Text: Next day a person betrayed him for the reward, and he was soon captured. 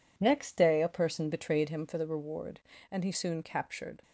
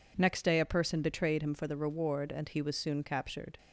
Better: second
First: skips "was"; at 3.1 s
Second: none

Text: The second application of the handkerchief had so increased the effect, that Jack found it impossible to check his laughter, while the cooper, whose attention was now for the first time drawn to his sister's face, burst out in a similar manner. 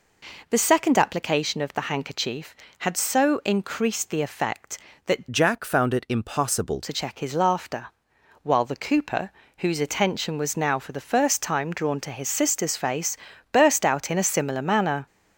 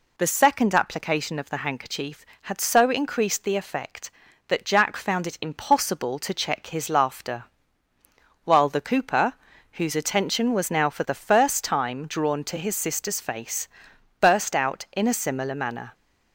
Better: second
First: changes voice from "Jack" to "impossible"; from 5.3 to 6.8 s; 1.5 s long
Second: none

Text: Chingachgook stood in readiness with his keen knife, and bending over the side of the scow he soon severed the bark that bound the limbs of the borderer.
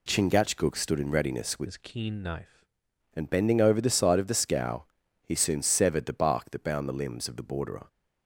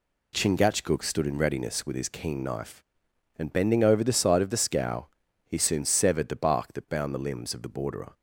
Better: second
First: changes voice from "his" to "knife"; from 1.6 to 2.6 s; 1.0 s long // pauses between "scow" and "he"; at 4.8 s; 0.40 s long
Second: pauses between "scow" and "he"; at 5.0 s; 0.40 s long

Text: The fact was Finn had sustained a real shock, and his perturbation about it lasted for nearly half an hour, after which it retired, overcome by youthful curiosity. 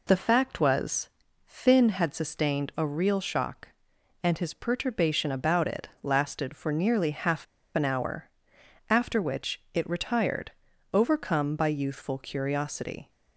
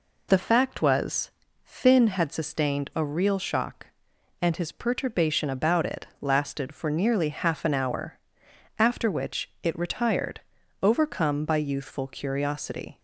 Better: second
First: pauses between "was" and "Finn"; slight; at 1.0 s; 0.36 s long // pauses between "half" and "an"; slight; at 7.4 s; 0.29 s long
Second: pauses between "was" and "Finn"; slight; at 1.3 s; 0.32 s long

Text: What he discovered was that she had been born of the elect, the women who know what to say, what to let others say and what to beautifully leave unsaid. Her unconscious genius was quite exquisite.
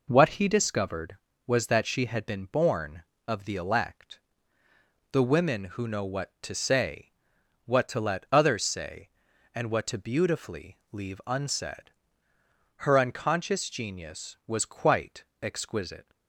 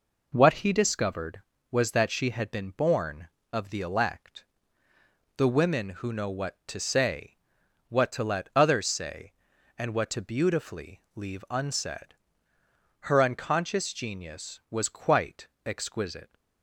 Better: neither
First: pauses between "quite" and "exquisite"; slight; at 15.2 s; 0.18 s long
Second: pauses between "quite" and "exquisite"; slight; at 15.4 s; 0.18 s long

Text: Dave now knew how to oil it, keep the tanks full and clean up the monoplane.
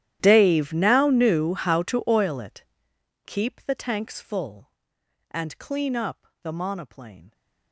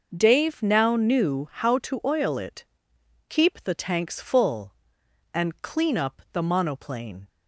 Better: second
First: gets quieter; strong; throughout; 24 dB // pauses between "up" and "the"; slight; at 6.2 s; 0.16 s long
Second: none

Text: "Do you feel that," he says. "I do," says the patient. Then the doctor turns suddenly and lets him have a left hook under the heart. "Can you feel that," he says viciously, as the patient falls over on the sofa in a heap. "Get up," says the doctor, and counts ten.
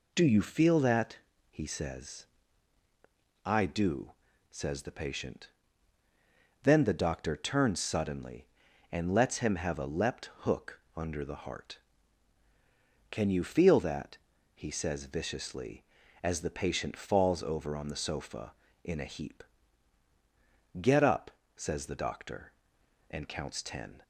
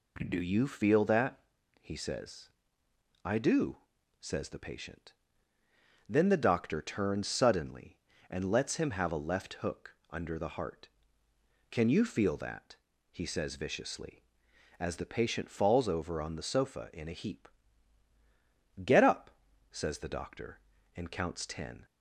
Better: second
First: says "leapt" for "left"; at 9.8 s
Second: none

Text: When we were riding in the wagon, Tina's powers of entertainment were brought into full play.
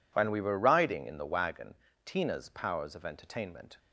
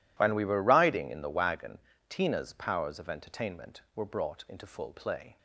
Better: second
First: stops before "were brought into full play"; at 3.7 s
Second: none

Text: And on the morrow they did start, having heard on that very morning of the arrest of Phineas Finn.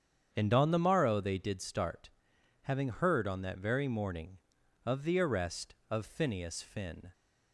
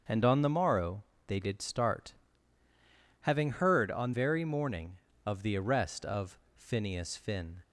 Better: first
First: starts louder than the rest; strong; until 1.3 s; 8 dB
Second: starts louder than the rest; until 1.3 s; 7 dB // pauses between "morrow" and "they"; slight; at 1.0 s; 0.24 s long // skips "that"; at 4.1 s // pauses between "of" and "Phineas"; slight; at 6.3 s; 0.16 s long

